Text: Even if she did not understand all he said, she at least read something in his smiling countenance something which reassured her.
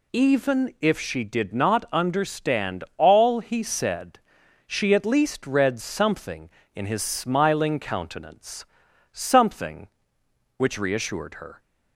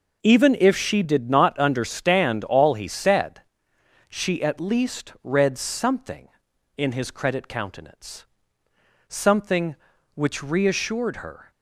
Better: first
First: pauses between "countenance" and "something"; noticeable; at 8.6 s; 0.48 s long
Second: says "credit" for "smiling"; at 7.1 s // pauses between "countenance" and "something"; noticeable; at 8.2 s; 0.86 s long

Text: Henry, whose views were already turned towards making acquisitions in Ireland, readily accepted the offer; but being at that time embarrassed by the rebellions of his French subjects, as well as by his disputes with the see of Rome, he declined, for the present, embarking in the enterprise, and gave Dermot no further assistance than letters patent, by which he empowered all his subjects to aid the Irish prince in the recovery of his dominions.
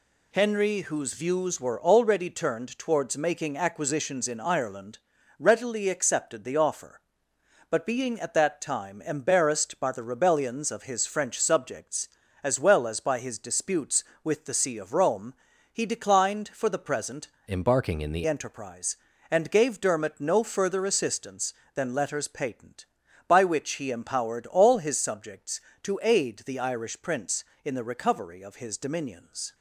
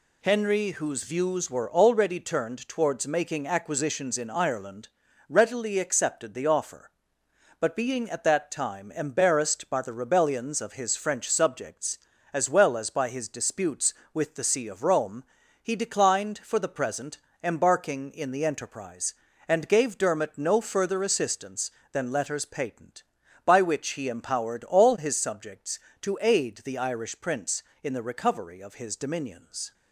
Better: second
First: changes voice from "embarking" to "the"; from 17.4 to 18.2 s; 0.8 s long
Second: none

